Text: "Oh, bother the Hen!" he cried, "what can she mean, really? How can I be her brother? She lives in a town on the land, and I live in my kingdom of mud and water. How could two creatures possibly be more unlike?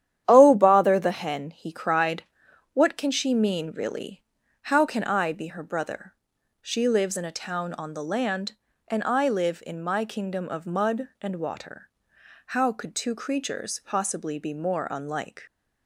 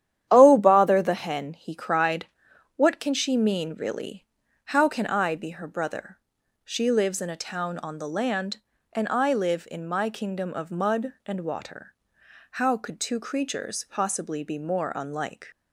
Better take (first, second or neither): neither